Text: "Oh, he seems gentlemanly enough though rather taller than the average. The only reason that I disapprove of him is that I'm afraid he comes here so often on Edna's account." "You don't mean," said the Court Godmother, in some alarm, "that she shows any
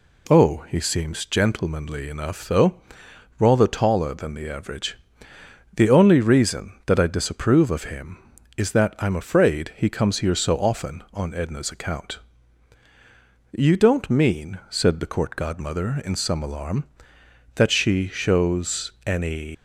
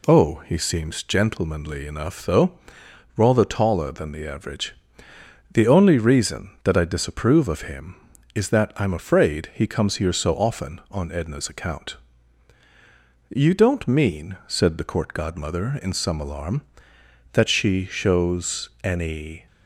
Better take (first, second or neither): second